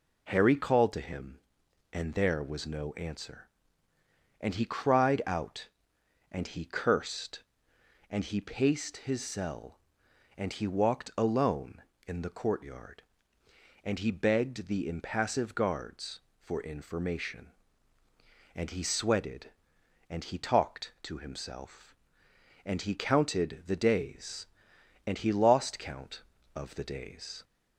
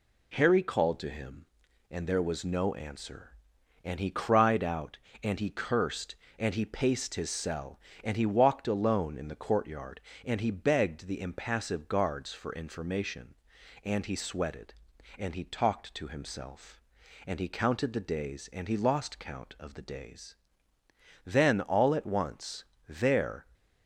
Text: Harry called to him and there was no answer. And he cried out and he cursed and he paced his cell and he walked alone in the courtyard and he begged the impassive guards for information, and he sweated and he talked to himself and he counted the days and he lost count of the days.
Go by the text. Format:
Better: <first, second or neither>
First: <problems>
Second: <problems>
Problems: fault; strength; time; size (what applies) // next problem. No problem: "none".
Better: first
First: none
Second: goes on to say "Then all at once there"; strong; from 21.2 s on; 2.1 s long